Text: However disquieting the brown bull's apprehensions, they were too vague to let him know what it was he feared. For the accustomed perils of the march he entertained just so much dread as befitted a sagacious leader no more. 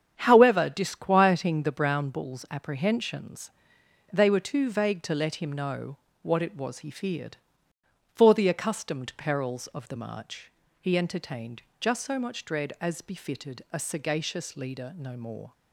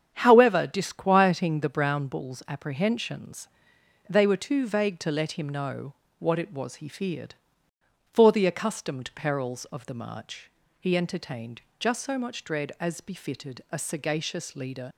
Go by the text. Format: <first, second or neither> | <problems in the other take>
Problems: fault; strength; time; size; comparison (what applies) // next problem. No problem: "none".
first | starts louder than the rest; strong; until 1.1 s; 8 dB; strong in the first // pauses between "know" and "what"; slight; at 5.9 s; 0.24 s long; slight in the first // pauses between "march" and "he"; slight; at 10.4 s; 0.32 s long; slight in the first // pauses between "entertained" and "just"; slight; at 11.6 s; 0.16 s long; slight in the first // stops before "no more"; at 14.9 s